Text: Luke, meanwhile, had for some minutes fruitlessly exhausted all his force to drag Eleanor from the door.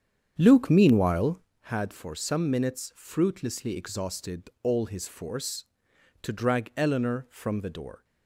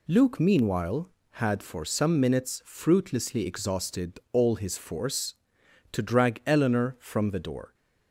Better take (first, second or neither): second